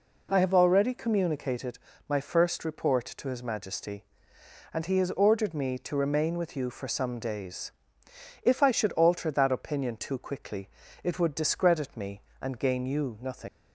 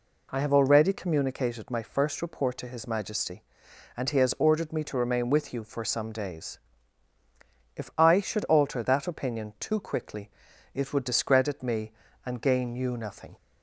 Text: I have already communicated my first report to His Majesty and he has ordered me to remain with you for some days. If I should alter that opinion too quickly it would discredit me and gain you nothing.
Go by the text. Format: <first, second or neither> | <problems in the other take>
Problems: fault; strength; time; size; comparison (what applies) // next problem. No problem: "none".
second | pauses between "communicated" and "my"; slight; at 1.7 s; 0.28 s long // pauses between "quickly" and "it"; slight; at 10.6 s; 0.34 s long; also in the second // leaves "nothing" unfinished; at 13.4 s; 95 ms